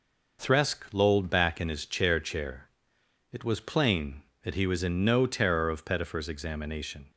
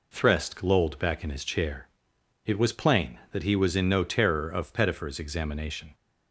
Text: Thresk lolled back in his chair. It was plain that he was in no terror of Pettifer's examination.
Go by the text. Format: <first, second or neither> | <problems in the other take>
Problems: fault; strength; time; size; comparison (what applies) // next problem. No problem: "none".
second | says "chair" twice; at 2.1 s